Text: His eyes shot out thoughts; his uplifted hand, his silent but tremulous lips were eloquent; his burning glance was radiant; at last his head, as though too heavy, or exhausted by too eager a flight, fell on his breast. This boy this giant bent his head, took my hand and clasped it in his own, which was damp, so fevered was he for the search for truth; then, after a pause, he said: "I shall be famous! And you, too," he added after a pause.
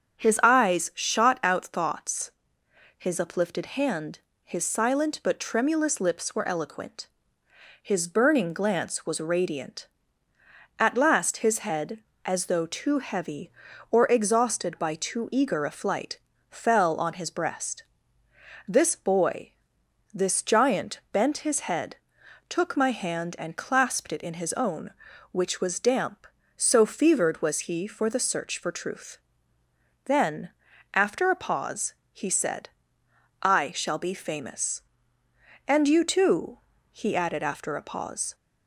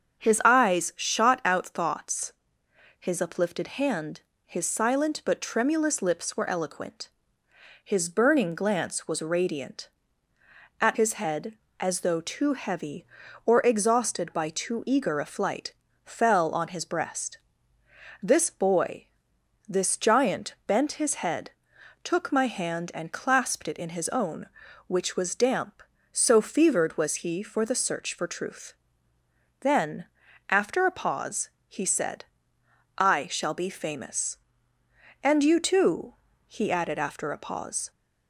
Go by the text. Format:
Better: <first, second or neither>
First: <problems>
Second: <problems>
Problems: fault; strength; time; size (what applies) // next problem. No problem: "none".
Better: first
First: starts louder than the rest; until 1.2 s; 7 dB // pauses between "boy" and "this"; noticeable; at 19.5 s; 0.62 s long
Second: starts louder than the rest; until 1.2 s; 7 dB // skips "last"; at 10.9 s // pauses between "boy" and "this"; noticeable; at 19.0 s; 0.62 s long